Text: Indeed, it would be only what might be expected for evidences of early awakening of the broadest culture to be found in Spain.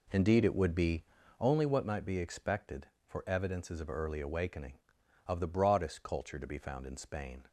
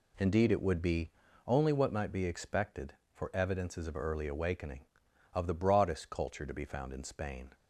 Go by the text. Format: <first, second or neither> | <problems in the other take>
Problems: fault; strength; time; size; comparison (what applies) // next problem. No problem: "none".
second | starts louder than the rest; until 1.5 s; 3.5 dB // pauses between "be" and "only"; slight; at 1.0 s; 0.36 s long; slight in the second